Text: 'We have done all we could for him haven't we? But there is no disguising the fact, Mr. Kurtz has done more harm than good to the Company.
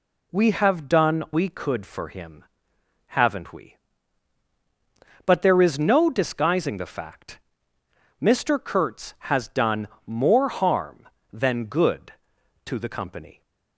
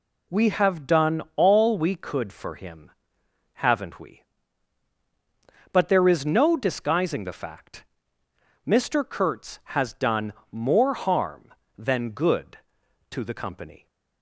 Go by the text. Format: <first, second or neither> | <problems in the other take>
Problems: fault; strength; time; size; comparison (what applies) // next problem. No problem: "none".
second | skips "all"; at 1.2 s // pauses between "him" and "haven't"; noticeable; at 2.4 s; 0.72 s long; noticeable in the second // pauses between "done" and "more"; slight; at 9.8 s; 0.16 s long; slight in the second